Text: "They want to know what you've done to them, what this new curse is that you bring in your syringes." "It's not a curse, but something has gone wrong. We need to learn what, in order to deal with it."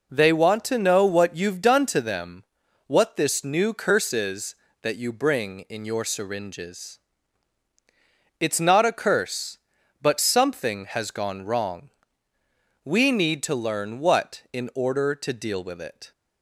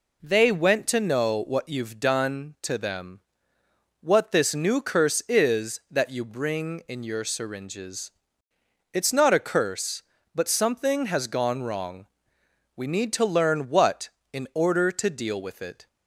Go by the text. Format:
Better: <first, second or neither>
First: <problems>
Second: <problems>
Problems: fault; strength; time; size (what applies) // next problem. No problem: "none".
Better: first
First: none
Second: says "went" for "want"; at 0.5 s